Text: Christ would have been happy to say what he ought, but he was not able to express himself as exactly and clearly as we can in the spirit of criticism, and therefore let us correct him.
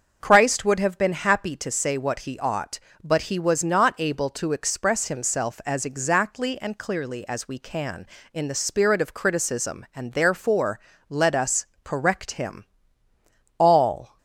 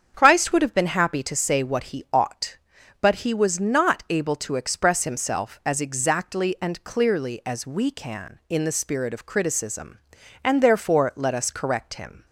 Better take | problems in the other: second | starts louder than the rest; until 1.2 s; 6.5 dB; strong in the second // pauses between "therefore" and "let"; slight; at 10.7 s; 0.30 s long // pauses between "us" and "correct"; slight; at 11.6 s; 0.18 s long // goes on to say "All"; from 13.5 s on; 0.60 s long

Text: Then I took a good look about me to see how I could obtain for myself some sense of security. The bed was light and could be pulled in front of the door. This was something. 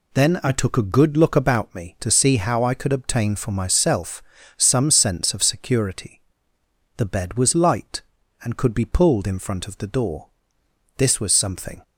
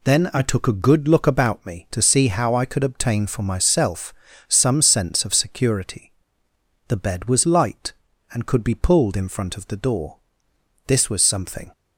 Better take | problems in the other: neither | pauses between "myself" and "some"; slight; the same in both

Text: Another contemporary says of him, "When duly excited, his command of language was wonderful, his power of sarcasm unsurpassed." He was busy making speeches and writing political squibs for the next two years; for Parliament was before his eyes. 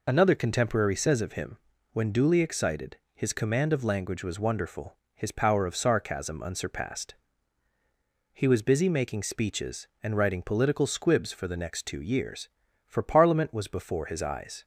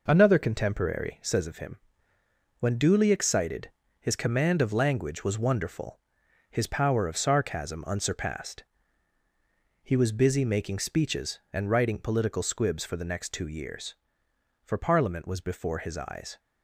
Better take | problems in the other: neither | none

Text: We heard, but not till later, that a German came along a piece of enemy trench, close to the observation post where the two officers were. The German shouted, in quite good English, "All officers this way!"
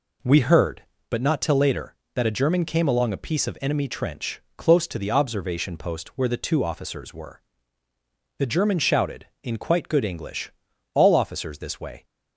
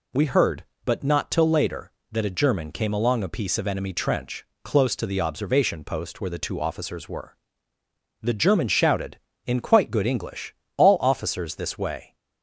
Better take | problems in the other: neither | none

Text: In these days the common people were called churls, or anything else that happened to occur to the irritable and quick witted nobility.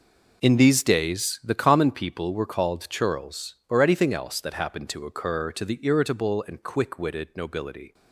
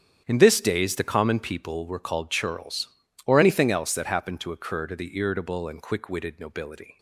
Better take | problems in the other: first | starts louder than the rest; strong; until 1.2 s; 9 dB // says "this" for "these"; at 0.3 s

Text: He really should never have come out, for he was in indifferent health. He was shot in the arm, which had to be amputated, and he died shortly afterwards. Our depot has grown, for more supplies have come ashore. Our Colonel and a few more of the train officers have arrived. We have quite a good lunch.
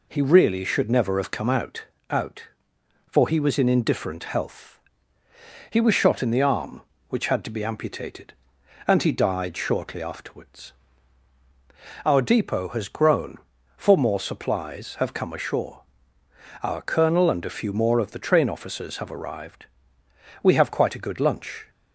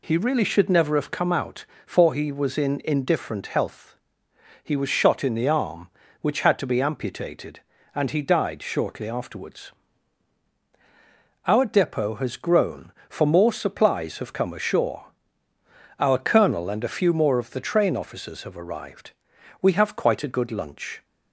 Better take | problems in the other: second | says "out" twice; at 2.0 s

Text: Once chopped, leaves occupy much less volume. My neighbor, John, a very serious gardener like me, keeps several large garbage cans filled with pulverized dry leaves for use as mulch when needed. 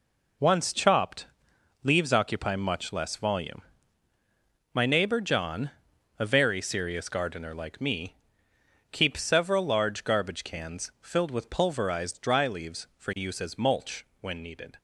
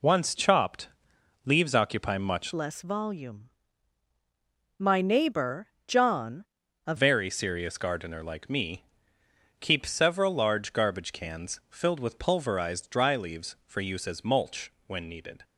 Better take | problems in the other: first | changes voice from "less" to "a"; from 2.5 to 6.9 s; 4.4 s long // pauses between "mulch" and "when"; slight; at 14.7 s; 0.16 s long; slight in the first

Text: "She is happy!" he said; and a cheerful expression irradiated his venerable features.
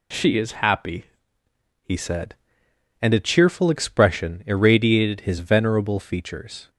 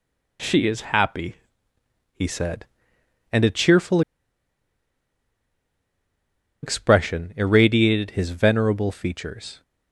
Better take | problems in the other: first | pauses between "cheerful" and "expression"; strong; at 4.0 s; 2.6 s long

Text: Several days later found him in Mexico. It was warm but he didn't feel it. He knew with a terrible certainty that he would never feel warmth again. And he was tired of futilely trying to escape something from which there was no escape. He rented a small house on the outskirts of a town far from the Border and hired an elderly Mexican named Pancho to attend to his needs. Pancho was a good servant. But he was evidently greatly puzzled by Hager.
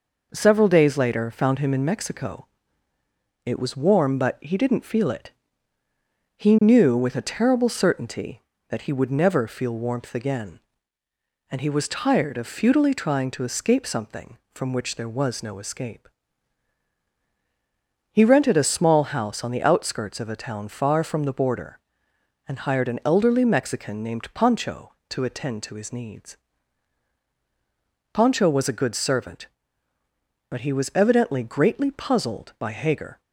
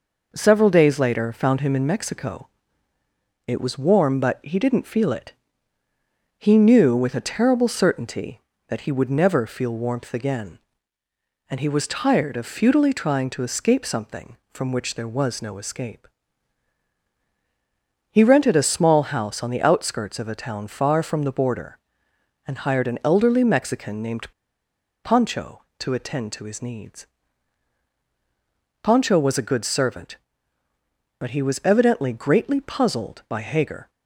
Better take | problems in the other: first | pauses between "named" and "Pancho"; noticeable; at 24.3 s; 0.72 s long

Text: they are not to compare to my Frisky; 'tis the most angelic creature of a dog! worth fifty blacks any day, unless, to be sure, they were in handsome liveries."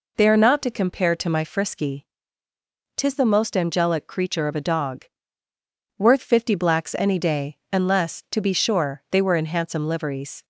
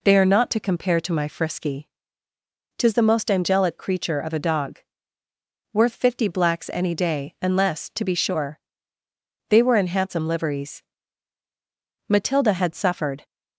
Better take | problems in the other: first | goes on to say "Matilda had suffered"; noticeable; from 12.0 s on; 1.1 s long

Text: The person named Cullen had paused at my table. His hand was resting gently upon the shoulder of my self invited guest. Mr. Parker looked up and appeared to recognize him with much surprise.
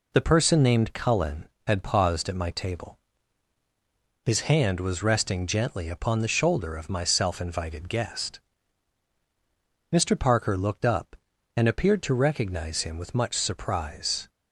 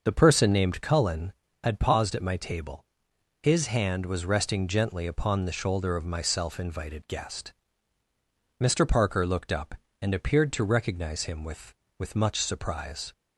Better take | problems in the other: first | starts louder than the rest; until 1.0 s; 6.5 dB // says "with" twice; at 11.9 s

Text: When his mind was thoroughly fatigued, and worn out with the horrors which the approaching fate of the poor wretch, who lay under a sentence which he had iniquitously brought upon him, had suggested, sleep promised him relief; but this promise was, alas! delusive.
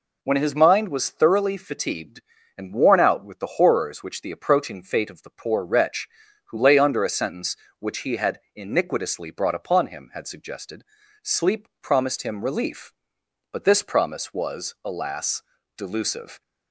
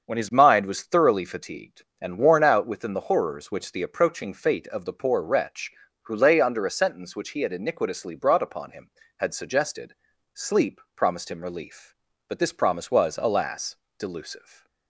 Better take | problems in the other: first | starts louder than the rest; until 1.0 s; 7 dB // says "within" for "with"; at 2.6 s

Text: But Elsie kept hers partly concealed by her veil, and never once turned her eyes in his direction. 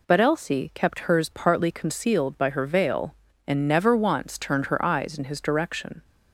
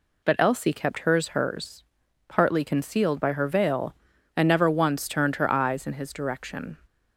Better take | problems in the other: first | says "hers" twice; at 1.2 s

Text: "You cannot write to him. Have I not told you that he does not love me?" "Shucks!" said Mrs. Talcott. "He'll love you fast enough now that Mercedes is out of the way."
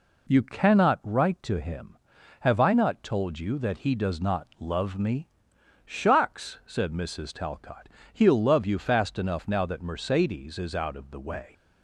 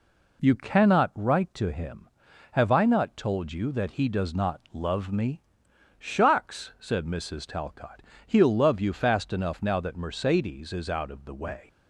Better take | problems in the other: neither | none

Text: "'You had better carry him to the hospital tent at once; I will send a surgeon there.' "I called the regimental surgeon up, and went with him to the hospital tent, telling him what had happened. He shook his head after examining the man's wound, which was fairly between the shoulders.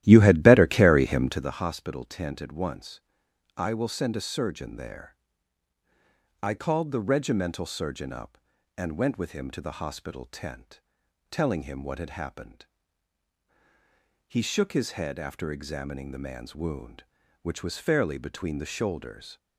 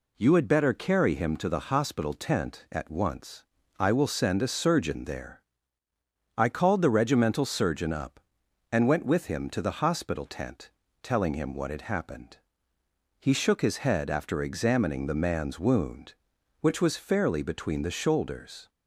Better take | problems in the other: second | starts louder than the rest; strong; until 1.6 s; 13.5 dB

